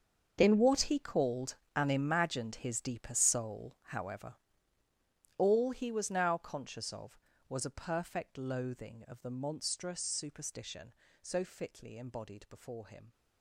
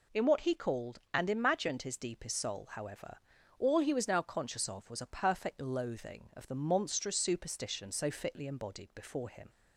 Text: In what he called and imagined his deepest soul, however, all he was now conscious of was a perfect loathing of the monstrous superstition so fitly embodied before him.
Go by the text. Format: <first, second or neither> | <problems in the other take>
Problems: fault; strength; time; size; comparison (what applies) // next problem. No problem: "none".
second | gets quieter; strong; throughout; 16 dB